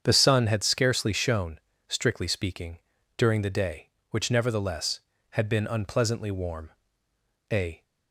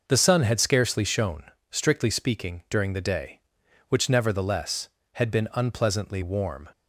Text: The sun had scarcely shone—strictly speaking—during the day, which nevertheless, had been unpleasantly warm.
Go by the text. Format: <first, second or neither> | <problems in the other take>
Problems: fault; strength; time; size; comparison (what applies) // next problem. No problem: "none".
second | starts louder than the rest; strong; until 1.0 s; 7.5 dB // goes on to say "A"; slight; from 7.5 s on; 0.32 s long